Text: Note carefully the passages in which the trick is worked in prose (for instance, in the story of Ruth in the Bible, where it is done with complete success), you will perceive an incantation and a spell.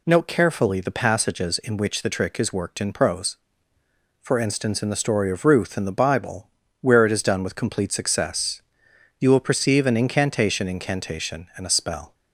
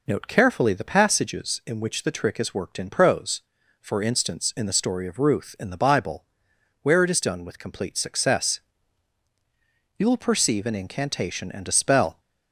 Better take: second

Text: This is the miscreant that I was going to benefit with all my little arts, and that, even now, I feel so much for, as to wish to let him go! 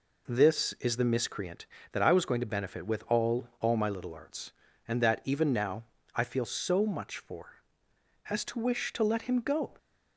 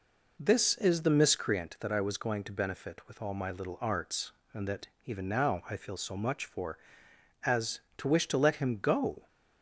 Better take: second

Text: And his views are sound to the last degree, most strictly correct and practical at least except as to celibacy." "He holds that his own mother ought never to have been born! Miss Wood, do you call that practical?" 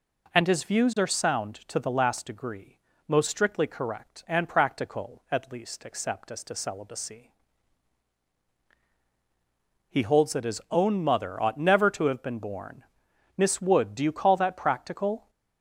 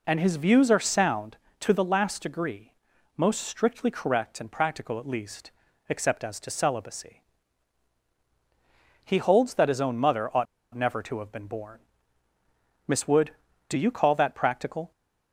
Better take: first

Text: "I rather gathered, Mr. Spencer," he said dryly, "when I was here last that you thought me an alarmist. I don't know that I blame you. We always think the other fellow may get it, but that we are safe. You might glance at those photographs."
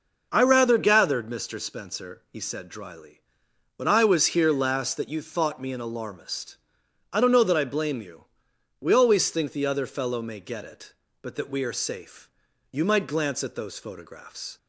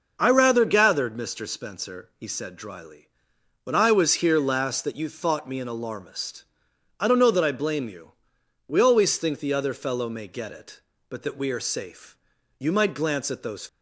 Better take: first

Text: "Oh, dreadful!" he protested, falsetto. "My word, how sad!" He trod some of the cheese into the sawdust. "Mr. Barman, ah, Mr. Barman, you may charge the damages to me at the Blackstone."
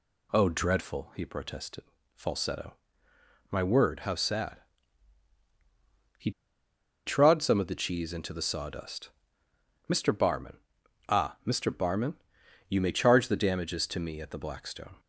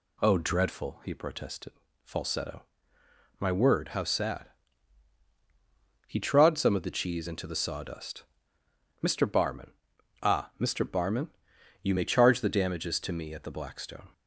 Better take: second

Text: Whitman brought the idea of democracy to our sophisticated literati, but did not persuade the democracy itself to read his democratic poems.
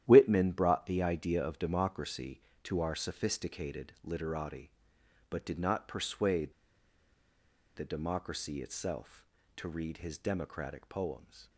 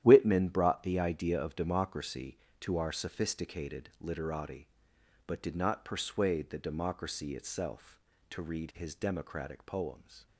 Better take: second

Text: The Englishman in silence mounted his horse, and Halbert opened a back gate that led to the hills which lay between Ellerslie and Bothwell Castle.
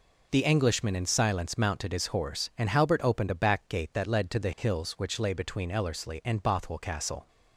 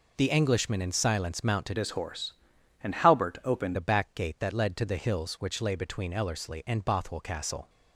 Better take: first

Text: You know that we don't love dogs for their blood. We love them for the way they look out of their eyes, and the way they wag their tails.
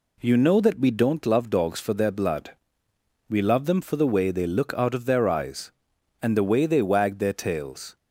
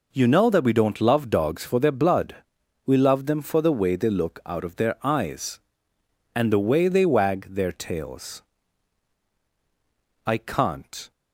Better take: first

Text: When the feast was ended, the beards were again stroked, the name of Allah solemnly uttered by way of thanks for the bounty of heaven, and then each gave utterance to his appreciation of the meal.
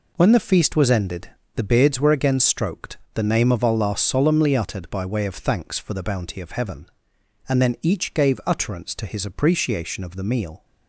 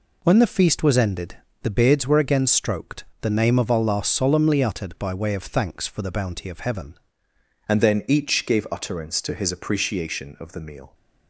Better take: first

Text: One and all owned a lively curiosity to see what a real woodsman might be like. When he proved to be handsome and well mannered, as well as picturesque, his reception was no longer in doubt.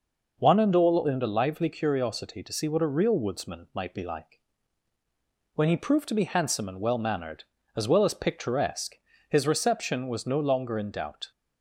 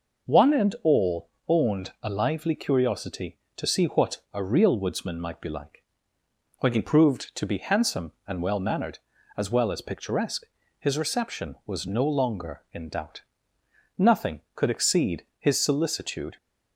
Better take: first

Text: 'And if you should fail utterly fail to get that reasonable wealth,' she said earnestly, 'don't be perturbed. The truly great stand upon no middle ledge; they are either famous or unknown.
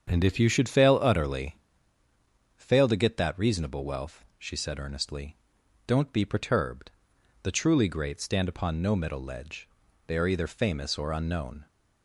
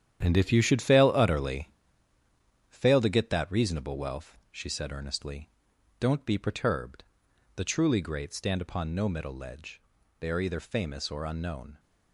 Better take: first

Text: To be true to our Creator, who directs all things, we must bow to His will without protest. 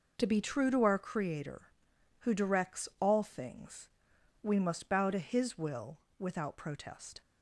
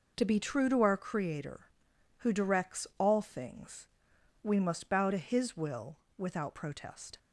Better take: neither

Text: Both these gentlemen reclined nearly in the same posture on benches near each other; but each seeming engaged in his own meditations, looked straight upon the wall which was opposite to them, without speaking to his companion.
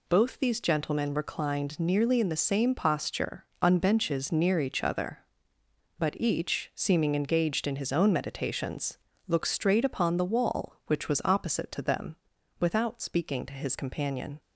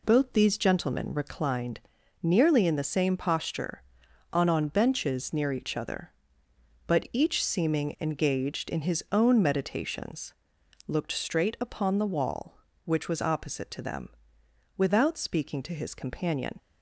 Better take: first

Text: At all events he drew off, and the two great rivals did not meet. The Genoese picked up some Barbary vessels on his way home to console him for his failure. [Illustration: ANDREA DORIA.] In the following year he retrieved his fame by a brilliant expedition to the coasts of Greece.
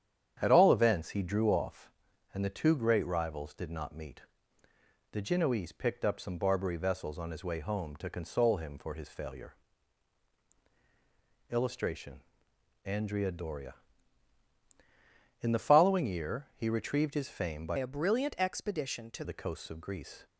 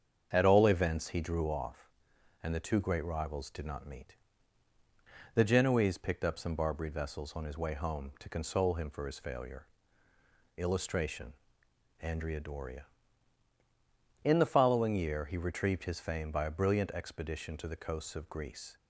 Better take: second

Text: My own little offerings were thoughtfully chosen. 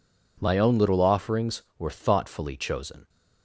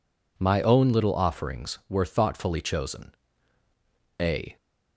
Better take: first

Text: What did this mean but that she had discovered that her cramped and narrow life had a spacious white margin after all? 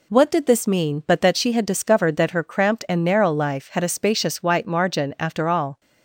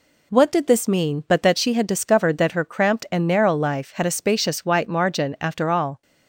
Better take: neither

